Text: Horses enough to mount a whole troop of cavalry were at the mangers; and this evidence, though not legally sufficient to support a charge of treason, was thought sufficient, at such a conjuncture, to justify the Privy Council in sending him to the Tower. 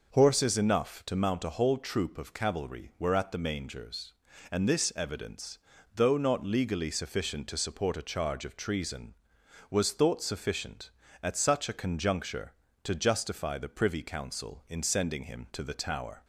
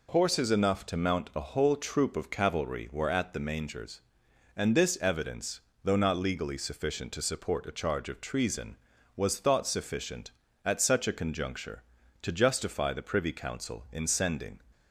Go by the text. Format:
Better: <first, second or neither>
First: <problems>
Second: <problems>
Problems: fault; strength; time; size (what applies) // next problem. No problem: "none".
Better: first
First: none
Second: stops before "him to the Tower"; at 14.7 s